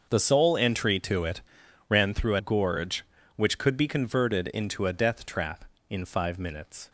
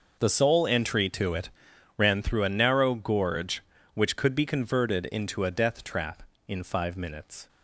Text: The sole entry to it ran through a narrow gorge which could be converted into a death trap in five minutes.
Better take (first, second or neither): second